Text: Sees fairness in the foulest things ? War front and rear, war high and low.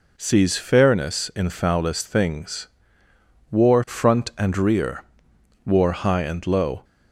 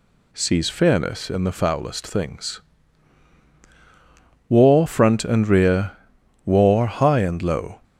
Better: second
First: skips "the"; at 1.5 s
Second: none

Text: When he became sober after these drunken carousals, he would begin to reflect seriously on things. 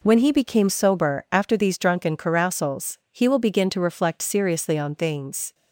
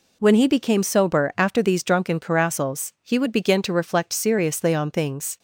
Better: second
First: says "will" for "would"; at 3.2 s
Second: none

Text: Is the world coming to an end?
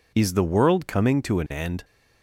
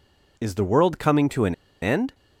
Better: first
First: none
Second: pauses between "an" and "end"; slight; at 1.5 s; 0.27 s long

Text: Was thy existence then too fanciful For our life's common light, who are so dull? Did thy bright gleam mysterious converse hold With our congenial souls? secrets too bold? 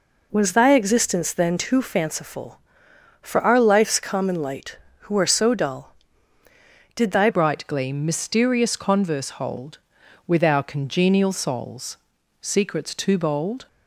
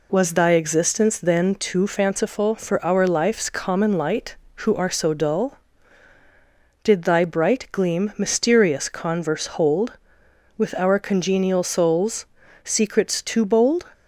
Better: second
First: changes voice at "bright"; from 7.2 s on; 6.4 s long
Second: none

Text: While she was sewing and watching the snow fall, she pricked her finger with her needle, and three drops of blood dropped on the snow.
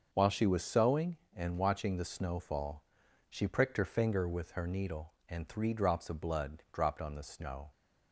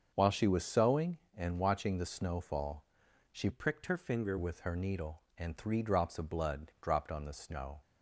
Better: first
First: starts louder than the rest; until 1.1 s; 6.5 dB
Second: starts louder than the rest; until 1.1 s; 7 dB // changes voice from "pricked" to "finger"; from 3.5 to 4.3 s; 0.8 s long

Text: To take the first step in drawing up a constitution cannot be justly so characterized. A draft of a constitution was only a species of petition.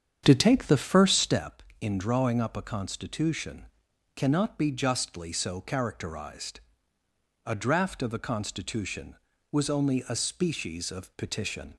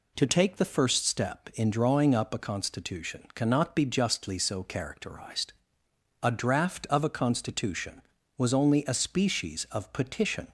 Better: second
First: starts louder than the rest; strong; until 1.4 s; 8 dB // pauses between "constitution" and "cannot"; noticeable; at 3.6 s; 0.50 s long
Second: none

